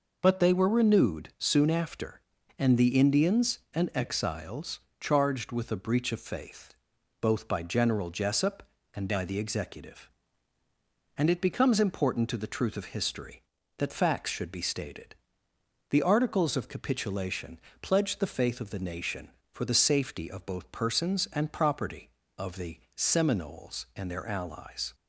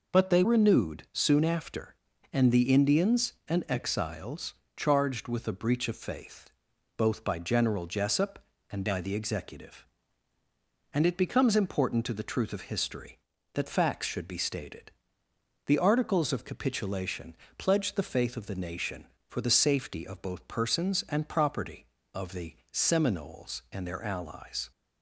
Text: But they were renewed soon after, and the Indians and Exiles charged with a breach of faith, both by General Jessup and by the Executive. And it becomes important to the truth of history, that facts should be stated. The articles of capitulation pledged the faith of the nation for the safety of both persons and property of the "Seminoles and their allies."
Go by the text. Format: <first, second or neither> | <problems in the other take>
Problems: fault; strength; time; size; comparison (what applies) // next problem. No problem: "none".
first | skips "were"; at 0.4 s // pauses between "Exiles" and "charged"; slight; at 4.5 s; 0.24 s long; slight in the first // pauses between "capitulation" and "pledged"; slight; at 17.3 s; 0.20 s long; slight in the first // pauses between "the" and "Seminoles"; slight; at 22.5 s; 0.18 s long; slight in the first